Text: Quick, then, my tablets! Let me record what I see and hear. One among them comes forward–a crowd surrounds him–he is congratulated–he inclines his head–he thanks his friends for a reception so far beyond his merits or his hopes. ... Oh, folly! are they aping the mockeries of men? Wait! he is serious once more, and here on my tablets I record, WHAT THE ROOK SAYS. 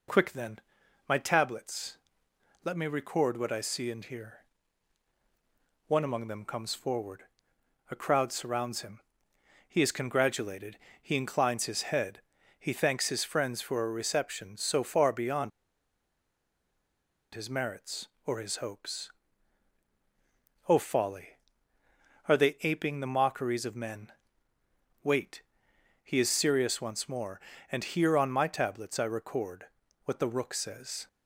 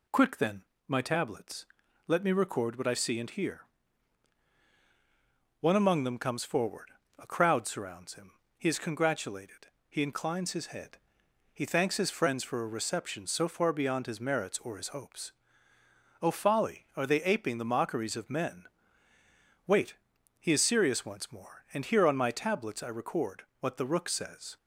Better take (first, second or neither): second